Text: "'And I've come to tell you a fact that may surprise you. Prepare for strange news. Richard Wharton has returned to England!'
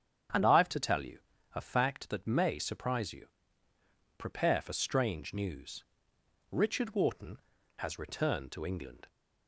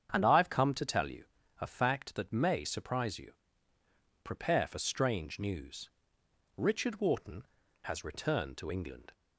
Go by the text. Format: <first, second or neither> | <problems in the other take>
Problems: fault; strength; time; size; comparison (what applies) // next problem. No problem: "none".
second | starts louder than the rest; strong; until 1.7 s; 8.5 dB; strong in the second // skips "come"; at 0.6 s // pauses between "you" and "a"; slight; at 1.1 s; 0.36 s long; slight in the second